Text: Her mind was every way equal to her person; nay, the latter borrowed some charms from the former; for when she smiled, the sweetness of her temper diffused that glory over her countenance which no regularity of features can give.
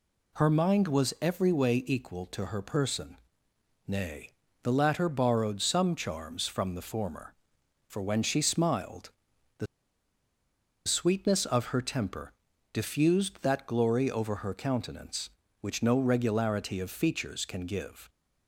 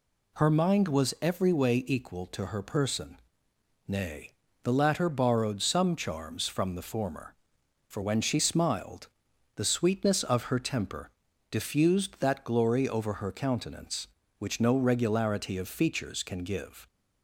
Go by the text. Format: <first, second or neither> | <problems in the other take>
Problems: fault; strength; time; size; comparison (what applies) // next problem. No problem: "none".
second | pauses between "the" and "sweetness"; at 9.6 s; 1.2 s long // pauses between "temper" and "diffused"; at 12.3 s; 0.40 s long; also in the second